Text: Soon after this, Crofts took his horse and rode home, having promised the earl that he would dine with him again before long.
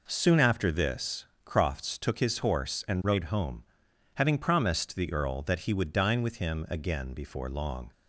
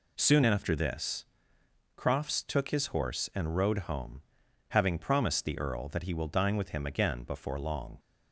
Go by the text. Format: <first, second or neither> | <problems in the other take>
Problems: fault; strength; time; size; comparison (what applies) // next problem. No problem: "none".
first | says "will" for "would"; at 6.1 s